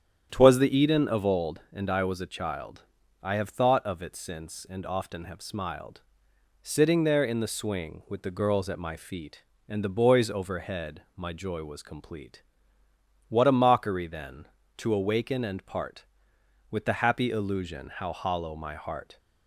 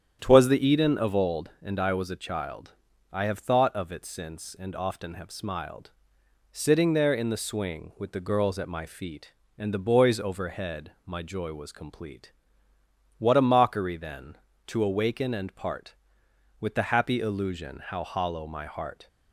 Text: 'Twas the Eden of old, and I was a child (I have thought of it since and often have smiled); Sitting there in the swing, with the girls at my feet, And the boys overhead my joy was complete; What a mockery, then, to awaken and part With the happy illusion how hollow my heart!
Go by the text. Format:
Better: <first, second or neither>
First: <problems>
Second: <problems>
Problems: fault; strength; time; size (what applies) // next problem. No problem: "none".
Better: neither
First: starts louder than the rest; strong; until 1.3 s; 9 dB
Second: starts louder than the rest; strong; until 1.2 s; 9 dB